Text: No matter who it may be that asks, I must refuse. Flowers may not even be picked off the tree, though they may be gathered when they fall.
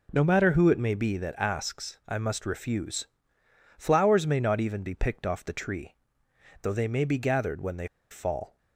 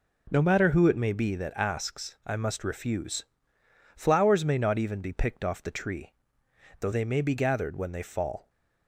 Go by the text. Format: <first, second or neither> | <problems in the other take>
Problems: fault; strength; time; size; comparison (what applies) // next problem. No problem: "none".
second | pauses between "they" and "fall"; slight; at 7.8 s; 0.24 s long